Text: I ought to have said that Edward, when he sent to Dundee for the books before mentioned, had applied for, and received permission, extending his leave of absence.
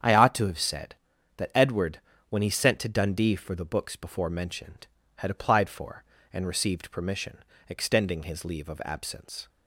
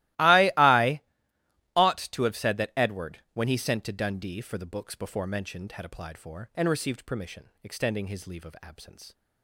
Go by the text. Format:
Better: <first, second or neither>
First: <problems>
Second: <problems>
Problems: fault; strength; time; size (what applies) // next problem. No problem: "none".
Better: first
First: starts louder than the rest; strong; until 1.4 s; 8.5 dB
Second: starts louder than the rest; strong; until 1.9 s; 17.5 dB // says "I" twice; at 0.5 s